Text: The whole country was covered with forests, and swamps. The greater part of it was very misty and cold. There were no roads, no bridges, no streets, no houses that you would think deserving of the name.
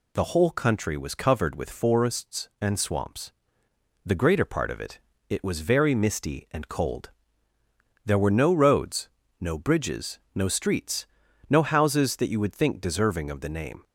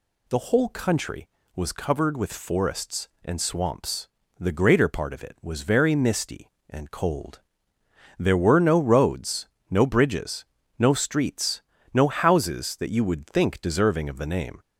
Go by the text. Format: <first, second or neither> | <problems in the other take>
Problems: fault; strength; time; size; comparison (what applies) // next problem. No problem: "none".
second | says "it" twice; at 5.2 s